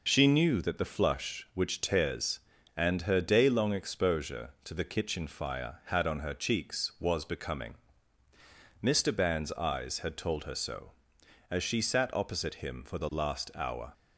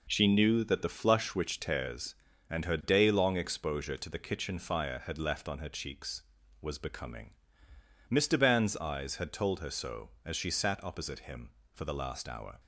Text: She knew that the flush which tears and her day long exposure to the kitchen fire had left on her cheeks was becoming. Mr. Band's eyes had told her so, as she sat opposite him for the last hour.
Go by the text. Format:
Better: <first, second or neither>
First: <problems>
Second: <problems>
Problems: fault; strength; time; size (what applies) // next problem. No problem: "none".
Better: second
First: skips "left"; at 6.0 s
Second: none